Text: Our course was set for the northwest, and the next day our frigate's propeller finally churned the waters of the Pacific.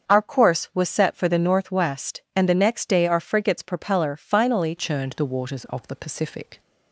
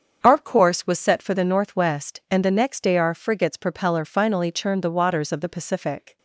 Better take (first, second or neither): second